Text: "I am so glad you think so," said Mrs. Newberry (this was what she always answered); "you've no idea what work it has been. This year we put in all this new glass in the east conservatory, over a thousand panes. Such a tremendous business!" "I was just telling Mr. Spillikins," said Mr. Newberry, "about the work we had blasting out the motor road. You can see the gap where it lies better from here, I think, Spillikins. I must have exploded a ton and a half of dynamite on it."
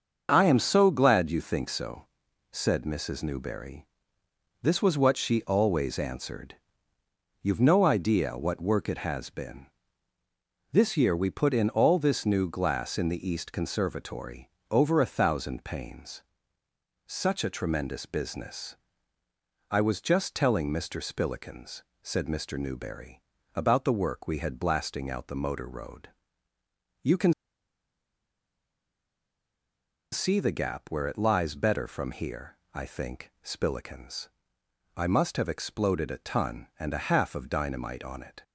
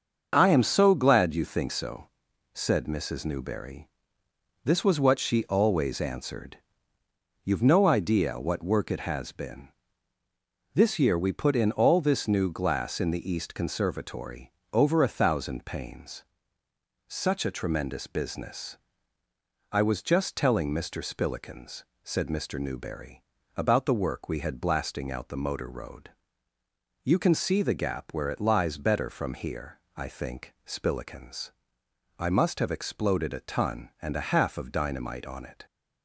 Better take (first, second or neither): second